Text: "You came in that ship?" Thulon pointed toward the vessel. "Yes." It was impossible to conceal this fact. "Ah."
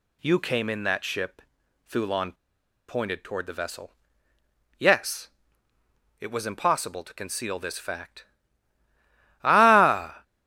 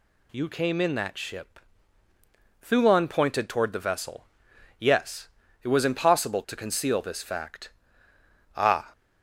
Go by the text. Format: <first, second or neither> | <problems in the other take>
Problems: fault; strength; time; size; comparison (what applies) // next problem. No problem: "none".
second | pauses between "Thulon" and "pointed"; noticeable; at 2.3 s; 0.53 s long